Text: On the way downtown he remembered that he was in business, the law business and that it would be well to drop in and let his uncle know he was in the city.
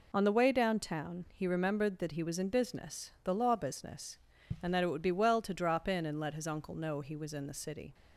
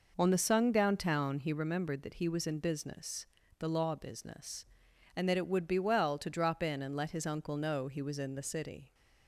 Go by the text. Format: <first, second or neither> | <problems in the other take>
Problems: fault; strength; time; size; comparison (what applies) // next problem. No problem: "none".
first | says "sung" for "way"; at 0.3 s